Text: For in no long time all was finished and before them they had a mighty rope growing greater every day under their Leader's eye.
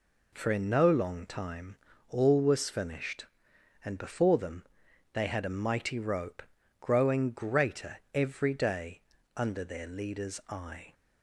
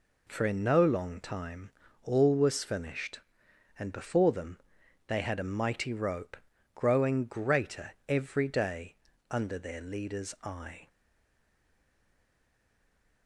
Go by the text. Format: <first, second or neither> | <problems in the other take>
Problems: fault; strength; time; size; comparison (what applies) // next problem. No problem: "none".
first | pauses between "time" and "all"; slight; at 1.6 s; 0.34 s long; slight in the first // pauses between "them" and "they"; noticeable; at 4.5 s; 0.50 s long; noticeable in the first // pauses between "rope" and "growing"; at 6.3 s; 0.38 s long; also in the first // pauses between "greater" and "every"; slight; at 7.9 s; 0.16 s long; slight in the first // pauses between "day" and "under"; slight; at 8.9 s; 0.36 s long; slight in the first // stays silent after the last word; from 10.8 s on; 2.4 s long